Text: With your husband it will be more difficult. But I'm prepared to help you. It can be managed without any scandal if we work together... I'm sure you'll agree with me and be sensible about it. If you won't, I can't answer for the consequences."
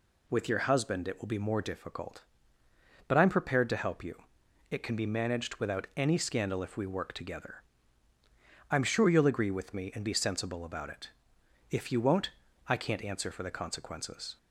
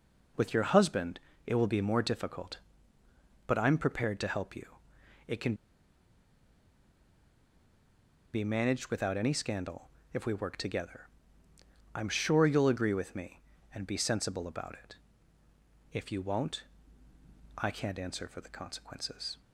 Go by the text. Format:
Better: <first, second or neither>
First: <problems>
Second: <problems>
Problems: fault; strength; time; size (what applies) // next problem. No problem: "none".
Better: first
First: none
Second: pauses between "husband" and "it"; slight; at 1.1 s; 0.26 s long // pauses between "can" and "be"; strong; at 5.5 s; 2.8 s long // pauses between "scandal" and "if"; slight; at 9.8 s; 0.24 s long